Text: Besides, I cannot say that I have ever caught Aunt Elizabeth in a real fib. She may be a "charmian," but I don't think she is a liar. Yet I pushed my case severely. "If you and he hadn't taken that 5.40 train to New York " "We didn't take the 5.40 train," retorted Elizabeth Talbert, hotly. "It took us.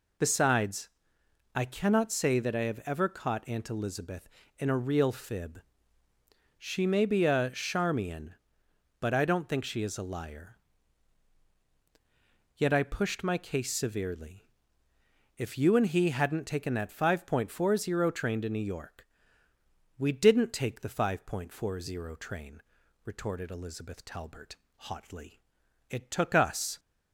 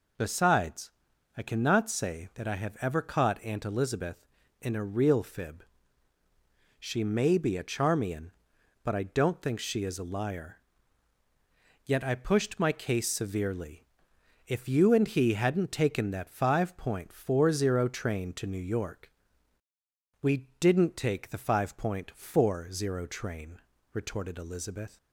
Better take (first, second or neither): first